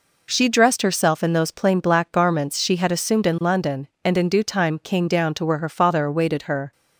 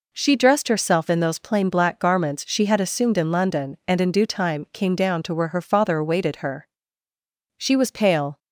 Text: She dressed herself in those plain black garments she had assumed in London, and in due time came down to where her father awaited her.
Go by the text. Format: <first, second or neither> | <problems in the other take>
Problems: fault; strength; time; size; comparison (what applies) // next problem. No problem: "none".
first | goes on to say "She was pale"; noticeable; from 7.5 s on; 0.80 s long